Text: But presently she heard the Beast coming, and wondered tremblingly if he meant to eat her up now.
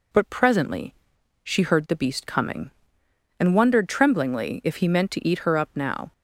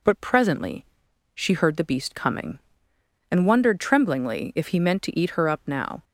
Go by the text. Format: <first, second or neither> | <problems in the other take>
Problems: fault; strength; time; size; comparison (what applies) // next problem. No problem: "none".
neither | pauses between "presently" and "she"; noticeable; the same in both